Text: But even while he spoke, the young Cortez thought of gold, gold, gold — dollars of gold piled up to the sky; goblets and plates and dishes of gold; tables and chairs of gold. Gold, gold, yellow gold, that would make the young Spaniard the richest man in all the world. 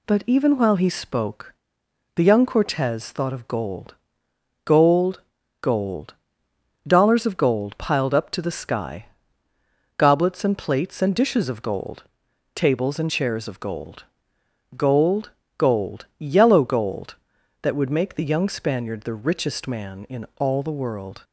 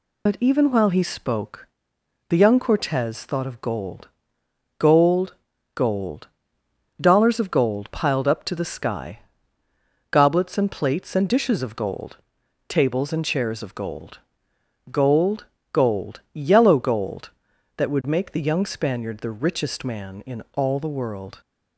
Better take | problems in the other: first | loses the start of "But"; at 0.2 s; 50 ms

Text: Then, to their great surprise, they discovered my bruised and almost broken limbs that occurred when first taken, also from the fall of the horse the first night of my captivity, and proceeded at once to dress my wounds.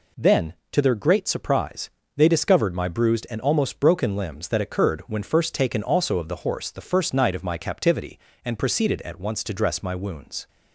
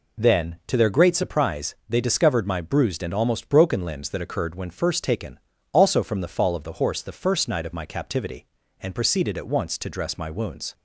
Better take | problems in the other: second | skips "from the fall"; at 6.1 s

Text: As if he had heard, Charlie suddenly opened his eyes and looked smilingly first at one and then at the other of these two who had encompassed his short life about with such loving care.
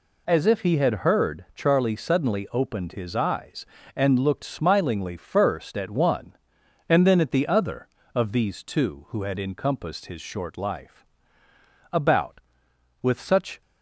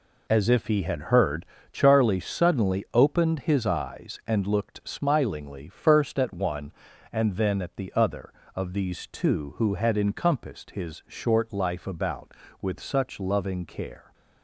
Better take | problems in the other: second | pauses between "life" and "about"; noticeable; at 11.0 s; 0.86 s long // stops before "loving care"; at 13.6 s

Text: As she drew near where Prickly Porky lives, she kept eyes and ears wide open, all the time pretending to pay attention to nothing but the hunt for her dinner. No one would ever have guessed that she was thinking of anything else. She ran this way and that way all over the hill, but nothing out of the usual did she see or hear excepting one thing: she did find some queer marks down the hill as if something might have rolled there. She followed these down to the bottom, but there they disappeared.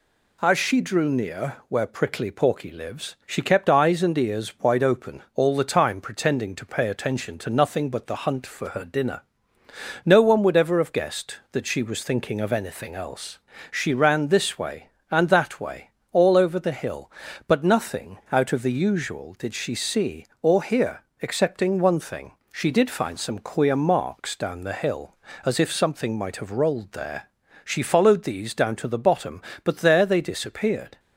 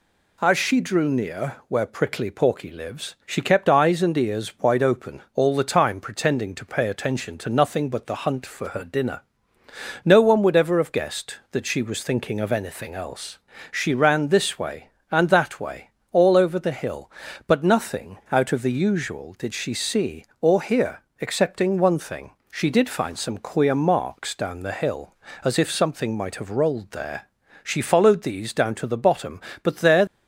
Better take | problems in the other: first | pauses between "way" and "all"; slight; at 15.8 s; 0.22 s long; slight in the first // pauses between "hear" and "excepting"; slight; at 21.0 s; 0.18 s long; slight in the first // stops before "they disappeared"; at 30.0 s

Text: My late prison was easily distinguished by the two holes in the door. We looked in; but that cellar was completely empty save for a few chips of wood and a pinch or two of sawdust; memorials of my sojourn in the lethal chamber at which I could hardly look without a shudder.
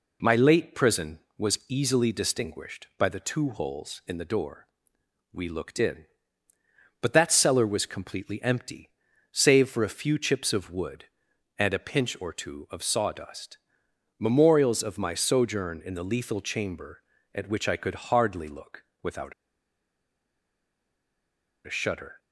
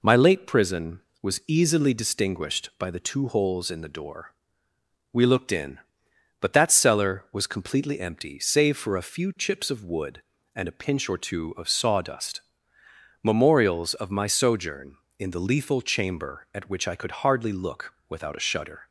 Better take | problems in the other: second | pauses between "empty" and "save"; at 8.9 s; 0.40 s long // pauses between "look" and "without"; slight; at 18.8 s; 0.16 s long; slight in the second // pauses between "without" and "a"; strong; at 19.3 s; 2.3 s long

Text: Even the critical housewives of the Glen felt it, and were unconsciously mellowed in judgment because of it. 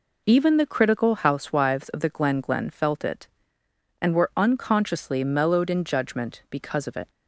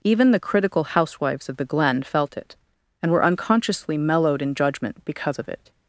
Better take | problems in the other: second | says "Glen" twice; at 2.3 s

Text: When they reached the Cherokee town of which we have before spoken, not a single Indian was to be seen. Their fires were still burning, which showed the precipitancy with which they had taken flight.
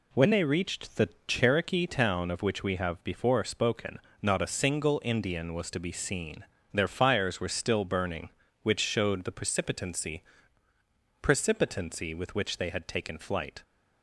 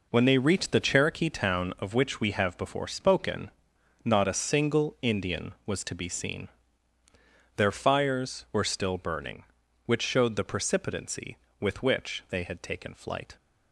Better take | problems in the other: second | pauses between "the" and "Cherokee"; slight; at 1.0 s; 0.20 s long // says "precipitancy" twice; at 11.2 s

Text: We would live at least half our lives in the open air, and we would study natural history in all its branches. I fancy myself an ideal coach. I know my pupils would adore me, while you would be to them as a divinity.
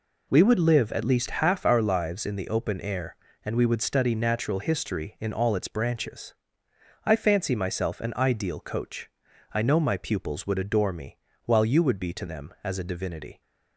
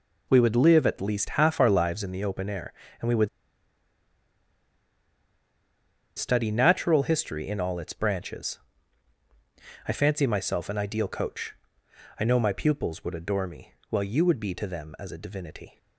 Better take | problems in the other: first | pauses between "would" and "study"; strong; at 3.2 s; 2.8 s long

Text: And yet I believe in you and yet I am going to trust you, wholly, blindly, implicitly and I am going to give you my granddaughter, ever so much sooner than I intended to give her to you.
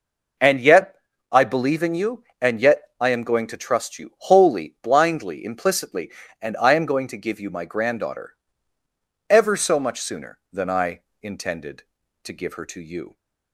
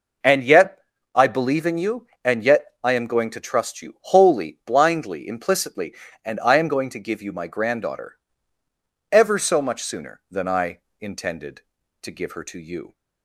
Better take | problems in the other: neither | pauses between "yet" and "I"; slight; the same in both // pauses between "yet" and "I"; slight; the same in both // pauses between "I" and "intended"; slight; the same in both

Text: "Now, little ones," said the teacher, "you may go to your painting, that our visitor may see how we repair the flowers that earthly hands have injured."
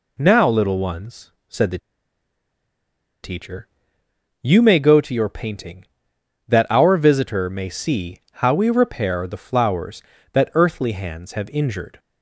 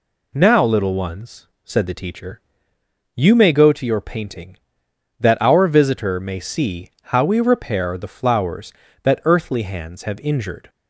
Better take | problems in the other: second | pauses between "the" and "teacher"; strong; at 1.7 s; 1.4 s long

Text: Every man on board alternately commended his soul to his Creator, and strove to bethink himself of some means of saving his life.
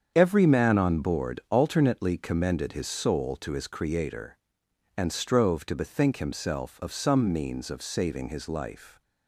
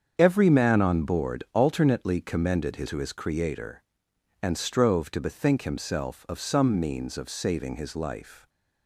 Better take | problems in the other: first | starts louder than the rest; strong; until 1.1 s; 7.5 dB; strong in the first // skips "soul"; at 2.8 s

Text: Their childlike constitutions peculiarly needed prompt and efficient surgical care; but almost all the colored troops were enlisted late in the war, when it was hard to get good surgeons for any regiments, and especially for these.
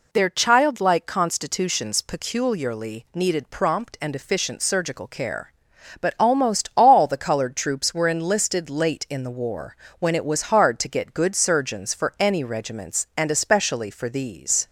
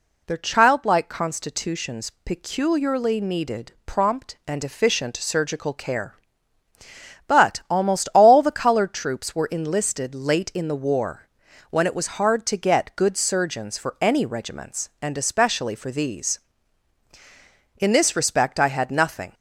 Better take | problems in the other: first | goes on to say "In this respect I had nothing"; from 17.7 s on; 1.5 s long

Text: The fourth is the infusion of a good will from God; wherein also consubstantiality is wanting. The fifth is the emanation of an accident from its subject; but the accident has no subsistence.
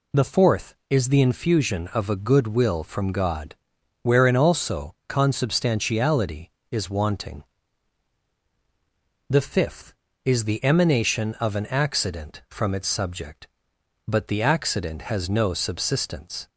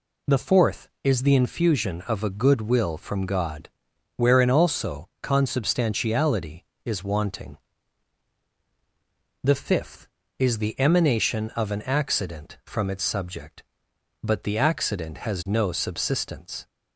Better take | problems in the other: neither | none

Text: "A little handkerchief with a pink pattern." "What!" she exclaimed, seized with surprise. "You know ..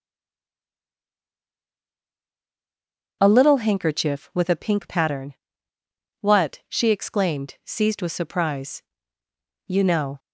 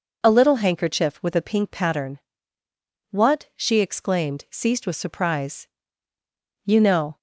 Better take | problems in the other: second | stays silent before the first word; strong; until 3.2 s; 3.2 s long // starts louder than the rest; noticeable; until 4.2 s; 6 dB

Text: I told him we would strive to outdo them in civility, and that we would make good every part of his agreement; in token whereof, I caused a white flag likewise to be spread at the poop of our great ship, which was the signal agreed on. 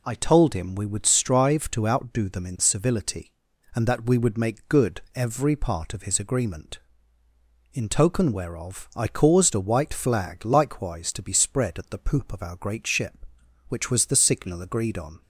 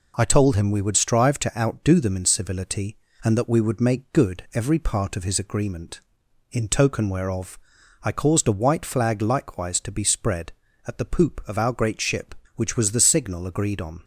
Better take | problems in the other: neither | none

